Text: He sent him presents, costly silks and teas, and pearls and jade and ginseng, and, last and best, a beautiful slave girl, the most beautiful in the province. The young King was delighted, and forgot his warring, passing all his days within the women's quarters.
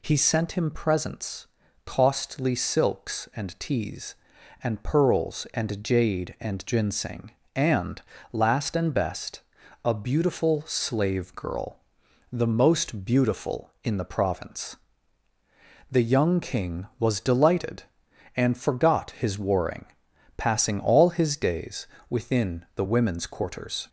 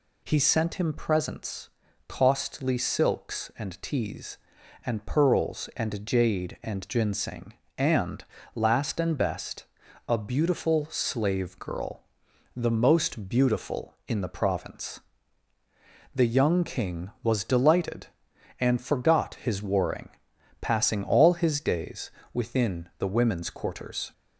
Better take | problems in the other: neither | pauses between "days" and "within"; slight; the same in both

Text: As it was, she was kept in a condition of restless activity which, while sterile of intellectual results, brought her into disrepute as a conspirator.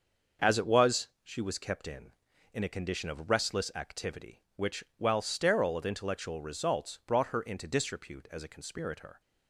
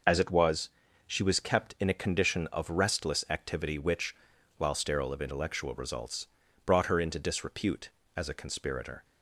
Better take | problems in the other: second | starts louder than the rest; until 1.5 s; 6.5 dB // says "in" twice; at 2.5 s

